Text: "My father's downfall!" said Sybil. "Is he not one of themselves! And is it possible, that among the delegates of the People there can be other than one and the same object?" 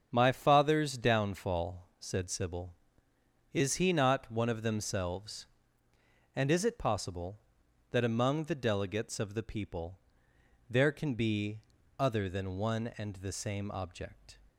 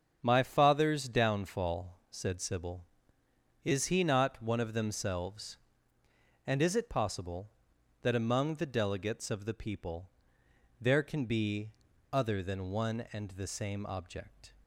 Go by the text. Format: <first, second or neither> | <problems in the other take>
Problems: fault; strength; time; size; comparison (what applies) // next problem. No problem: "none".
neither | starts louder than the rest; strong; the same in both // pauses between "People" and "there"; noticeable; the same in both // pauses between "be" and "other"; the same in both